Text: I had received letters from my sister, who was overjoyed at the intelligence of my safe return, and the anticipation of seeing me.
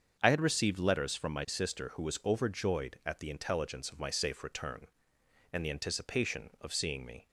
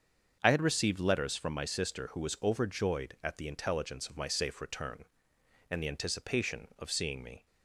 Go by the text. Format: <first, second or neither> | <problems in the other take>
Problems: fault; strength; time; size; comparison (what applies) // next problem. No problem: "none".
neither | starts louder than the rest; the same in both